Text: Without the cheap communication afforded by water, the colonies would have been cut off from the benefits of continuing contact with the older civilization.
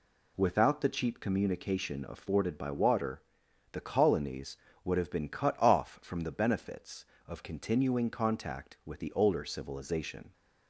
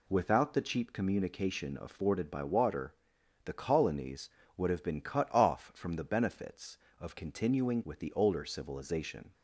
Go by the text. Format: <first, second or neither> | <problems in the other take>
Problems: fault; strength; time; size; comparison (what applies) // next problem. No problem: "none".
first | skips "contact"; at 7.8 s